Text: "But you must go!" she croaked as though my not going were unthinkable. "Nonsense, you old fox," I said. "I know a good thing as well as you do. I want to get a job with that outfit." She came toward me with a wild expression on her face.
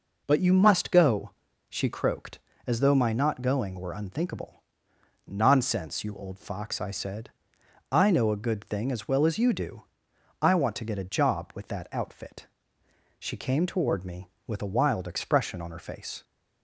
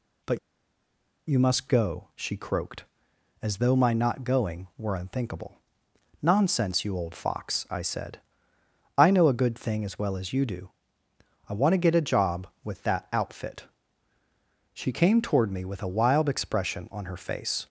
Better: first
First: none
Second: pauses between "But" and "you"; noticeable; at 0.3 s; 0.89 s long

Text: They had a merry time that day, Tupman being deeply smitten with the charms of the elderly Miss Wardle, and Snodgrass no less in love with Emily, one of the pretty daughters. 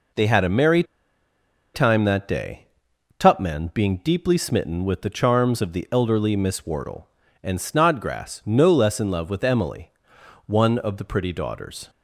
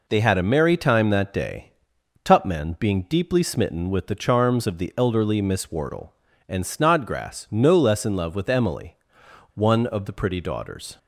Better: second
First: pauses between "merry" and "time"; noticeable; at 0.8 s; 0.91 s long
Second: none

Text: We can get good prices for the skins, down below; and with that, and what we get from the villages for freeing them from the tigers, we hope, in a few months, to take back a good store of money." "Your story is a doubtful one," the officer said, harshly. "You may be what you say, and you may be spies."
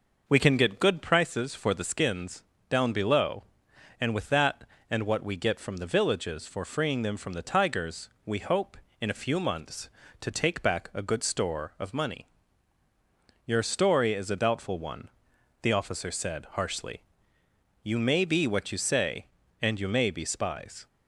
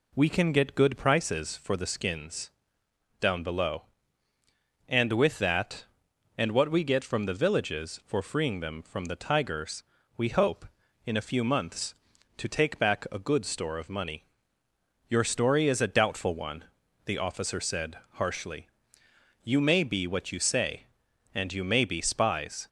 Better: second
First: starts louder than the rest; noticeable; until 1.2 s; 5.5 dB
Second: none

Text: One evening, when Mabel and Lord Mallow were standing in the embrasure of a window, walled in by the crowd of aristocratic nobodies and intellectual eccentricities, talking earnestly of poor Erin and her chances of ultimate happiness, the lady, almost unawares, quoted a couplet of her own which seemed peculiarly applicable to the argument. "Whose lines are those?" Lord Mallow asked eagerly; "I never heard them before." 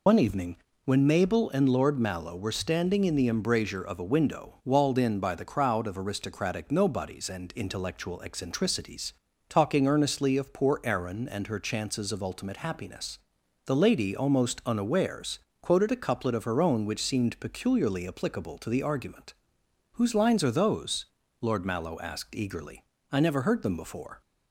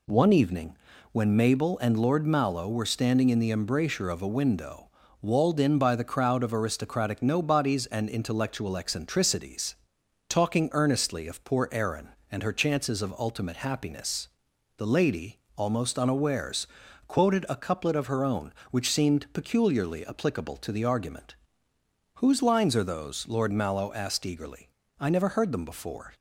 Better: second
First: loses the start of "One"; at 0.0 s; 80 ms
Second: none

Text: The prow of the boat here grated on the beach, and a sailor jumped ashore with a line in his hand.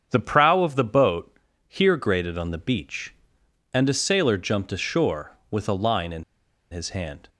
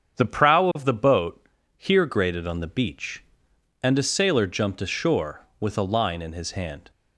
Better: second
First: starts louder than the rest; strong; until 1.1 s; 7.5 dB // pauses between "boat" and "here"; slight; at 1.3 s; 0.30 s long // pauses between "in" and "his"; noticeable; at 6.2 s; 0.48 s long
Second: starts louder than the rest; strong; until 1.2 s; 7.5 dB // pauses between "boat" and "here"; slight; at 1.4 s; 0.30 s long

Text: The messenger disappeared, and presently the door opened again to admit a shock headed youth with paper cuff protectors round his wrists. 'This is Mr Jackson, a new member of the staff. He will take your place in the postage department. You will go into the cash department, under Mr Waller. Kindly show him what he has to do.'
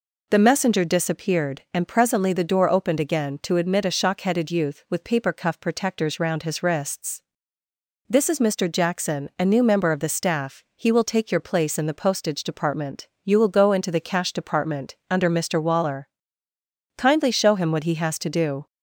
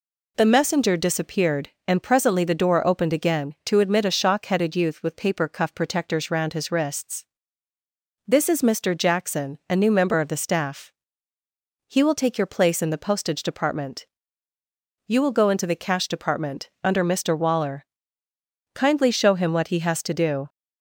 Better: neither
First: none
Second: none

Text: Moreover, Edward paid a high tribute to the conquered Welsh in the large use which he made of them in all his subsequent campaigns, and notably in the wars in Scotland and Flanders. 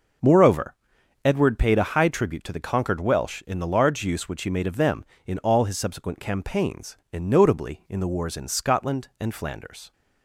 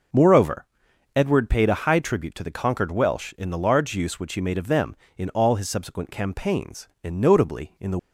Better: first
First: none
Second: stops before "wars in Scotland and Flanders"; at 7.9 s

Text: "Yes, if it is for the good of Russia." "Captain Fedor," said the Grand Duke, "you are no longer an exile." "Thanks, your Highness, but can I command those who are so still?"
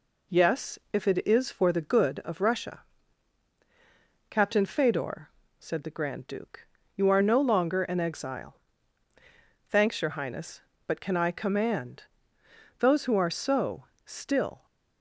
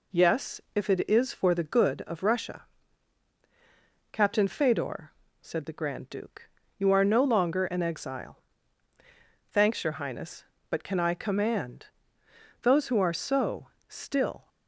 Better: neither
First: pauses between "command" and "those"; noticeable; at 12.0 s; 0.76 s long // pauses between "so" and "still"; slight; at 13.8 s; 0.20 s long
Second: pauses between "command" and "those"; noticeable; at 11.8 s; 0.76 s long // pauses between "so" and "still"; slight; at 13.6 s; 0.20 s long

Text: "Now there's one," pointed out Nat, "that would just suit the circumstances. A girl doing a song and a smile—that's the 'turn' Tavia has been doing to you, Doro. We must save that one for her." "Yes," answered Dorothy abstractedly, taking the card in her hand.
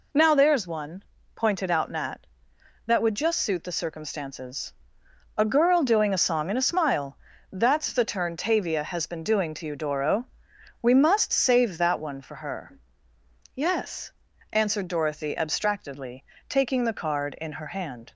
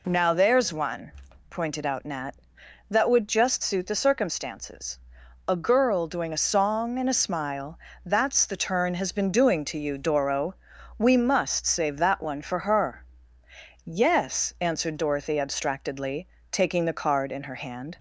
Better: first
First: none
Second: skips "Tavia"; at 8.9 s

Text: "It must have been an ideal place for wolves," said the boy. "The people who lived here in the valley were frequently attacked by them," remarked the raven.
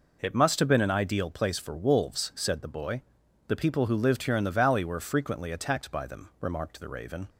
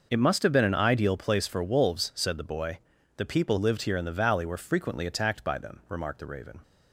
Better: first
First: none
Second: skips "who"; at 3.5 s

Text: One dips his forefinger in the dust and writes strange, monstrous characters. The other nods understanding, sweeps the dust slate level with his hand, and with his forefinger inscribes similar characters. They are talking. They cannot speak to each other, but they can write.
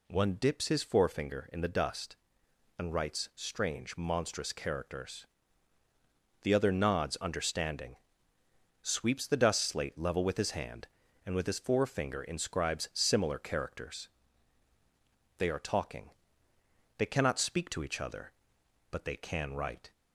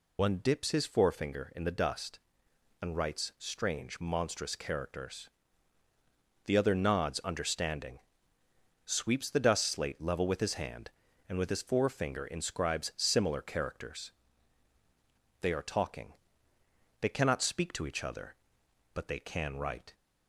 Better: first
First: none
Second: loses the start of "One"; at 0.1 s; 90 ms

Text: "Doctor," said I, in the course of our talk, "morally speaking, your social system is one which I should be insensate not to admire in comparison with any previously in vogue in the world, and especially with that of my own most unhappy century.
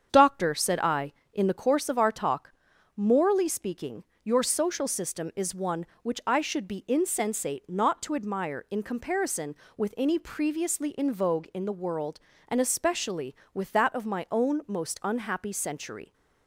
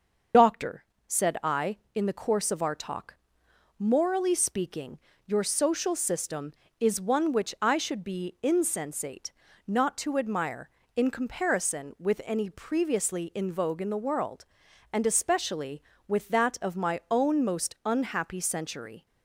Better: first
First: starts louder than the rest; strong; until 1.1 s; 7.5 dB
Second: loses the start of "Doctor"; at 0.3 s; 85 ms // starts louder than the rest; until 1.6 s; 6.5 dB // pauses between "insensate" and "not"; slight; at 9.3 s; 0.34 s long

